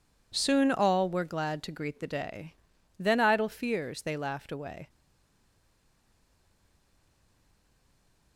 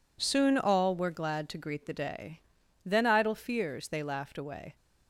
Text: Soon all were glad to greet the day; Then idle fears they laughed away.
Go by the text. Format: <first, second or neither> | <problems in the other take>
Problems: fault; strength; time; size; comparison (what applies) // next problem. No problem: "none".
second | stays silent after the last word; strong; from 4.8 s on; 3.5 s long